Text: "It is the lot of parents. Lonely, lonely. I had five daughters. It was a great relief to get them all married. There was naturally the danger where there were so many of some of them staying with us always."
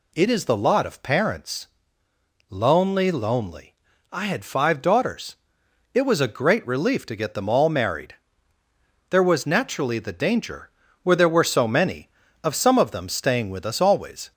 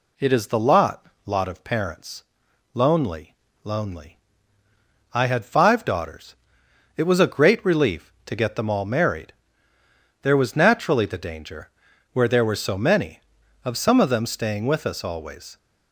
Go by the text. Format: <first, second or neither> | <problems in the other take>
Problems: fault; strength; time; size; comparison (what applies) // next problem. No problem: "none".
first | says "lot" twice; at 1.2 s // pauses between "danger" and "where"; at 11.6 s; 0.42 s long; slight in the first